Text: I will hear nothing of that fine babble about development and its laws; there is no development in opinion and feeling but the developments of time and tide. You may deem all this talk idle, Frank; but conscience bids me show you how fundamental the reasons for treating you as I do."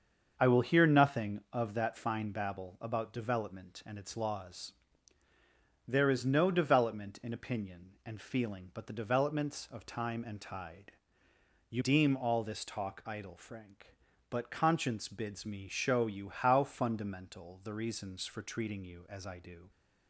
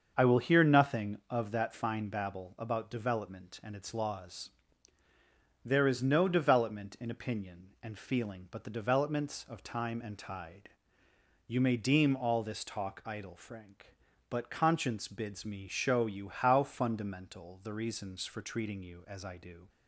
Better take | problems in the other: second | starts louder than the rest; until 1.3 s; 6.5 dB; also in the second // skips "may"; at 11.8 s

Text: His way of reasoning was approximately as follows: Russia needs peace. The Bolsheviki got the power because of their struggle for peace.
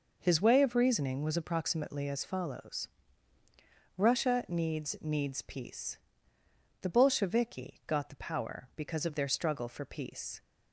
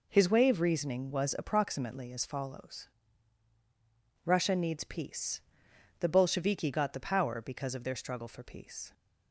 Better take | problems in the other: second | says "needs" twice; at 5.0 s

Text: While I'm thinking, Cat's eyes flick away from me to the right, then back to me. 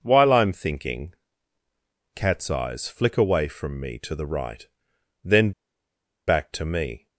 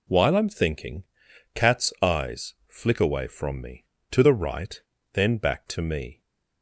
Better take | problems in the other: second | pauses between "then" and "back"; noticeable; at 5.5 s; 0.76 s long

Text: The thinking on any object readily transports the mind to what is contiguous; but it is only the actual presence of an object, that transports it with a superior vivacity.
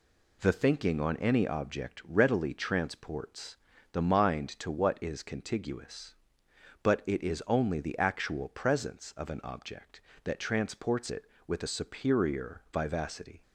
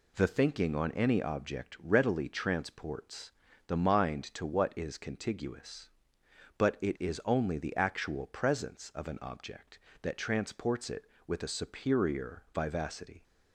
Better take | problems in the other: neither | pauses between "transports" and "the"; the same in both

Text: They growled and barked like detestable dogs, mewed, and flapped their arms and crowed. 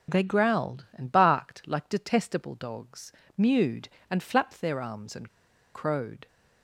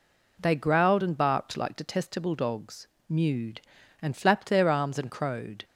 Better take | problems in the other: second | starts louder than the rest; until 1.2 s; 6.5 dB // pauses between "and" and "crowed"; at 5.2 s; 0.44 s long

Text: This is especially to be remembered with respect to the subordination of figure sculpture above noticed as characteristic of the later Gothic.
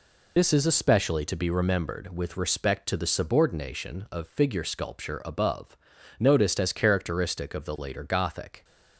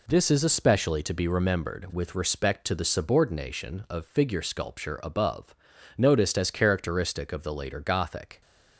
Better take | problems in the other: second | loses the start of "This"; at 0.3 s; 60 ms // pauses between "above" and "noticed"; at 5.7 s; 0.44 s long; also in the second

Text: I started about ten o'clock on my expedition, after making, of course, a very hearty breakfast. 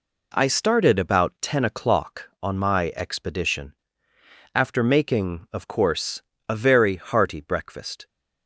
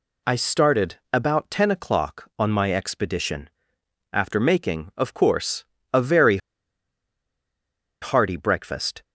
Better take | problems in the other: first | pauses between "very" and "hearty"; strong; at 6.3 s; 1.6 s long

